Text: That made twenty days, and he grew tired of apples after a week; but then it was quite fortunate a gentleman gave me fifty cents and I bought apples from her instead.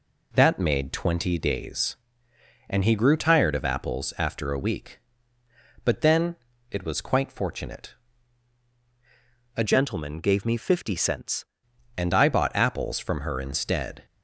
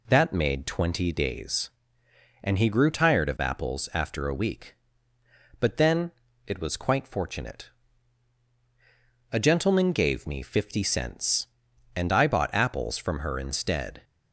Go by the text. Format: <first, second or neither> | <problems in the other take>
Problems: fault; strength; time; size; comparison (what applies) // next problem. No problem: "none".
second | pauses between "then" and "it"; slight; at 6.3 s; 0.34 s long; slight in the second // pauses between "fortunate" and "a"; strong; at 7.9 s; 1.6 s long; strong in the second // changes voice from "gentleman" to "cents"; from 9.6 to 11.4 s; 1.8 s long